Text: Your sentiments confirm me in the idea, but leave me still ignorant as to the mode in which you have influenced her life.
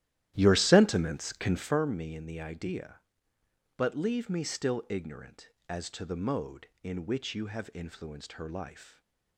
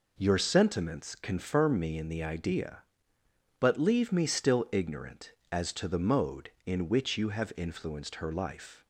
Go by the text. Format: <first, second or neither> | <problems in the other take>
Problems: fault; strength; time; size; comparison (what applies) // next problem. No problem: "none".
second | starts louder than the rest; strong; until 1.8 s; 13 dB // stays silent after the last word; slight; from 8.8 s on; 0.5 s long